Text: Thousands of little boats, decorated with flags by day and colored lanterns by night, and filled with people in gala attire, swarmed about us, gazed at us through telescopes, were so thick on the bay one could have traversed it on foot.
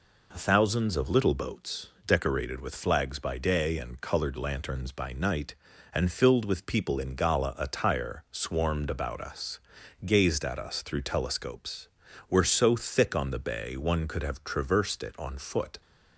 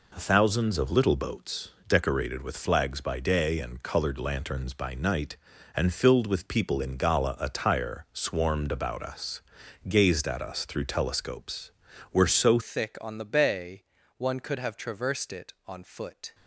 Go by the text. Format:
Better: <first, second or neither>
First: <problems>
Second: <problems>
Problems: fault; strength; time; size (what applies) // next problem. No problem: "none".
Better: first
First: none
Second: changes voice at "thick"; from 12.6 s on; 3.7 s long // pauses between "bay" and "one"; slight; at 13.8 s; 0.36 s long